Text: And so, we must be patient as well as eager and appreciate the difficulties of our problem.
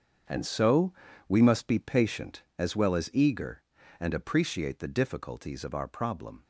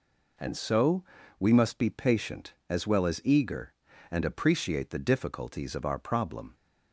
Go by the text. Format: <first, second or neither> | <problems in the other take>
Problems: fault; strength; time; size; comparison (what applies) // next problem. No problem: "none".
second | gets quieter; strong; throughout; 12 dB